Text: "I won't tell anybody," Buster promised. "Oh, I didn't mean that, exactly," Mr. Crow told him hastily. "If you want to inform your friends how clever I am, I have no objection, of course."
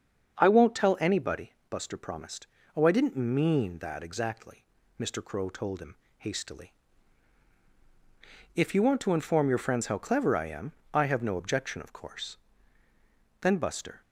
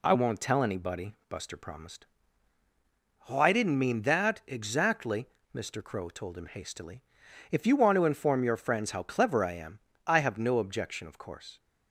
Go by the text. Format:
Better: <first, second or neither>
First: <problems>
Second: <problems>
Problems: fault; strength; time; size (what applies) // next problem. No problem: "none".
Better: second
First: starts louder than the rest; until 1.4 s; 7 dB // pauses between "him" and "hastily"; slight; at 5.9 s; 0.22 s long // goes on to say "Then Buster"; from 13.4 s on; 0.58 s long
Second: none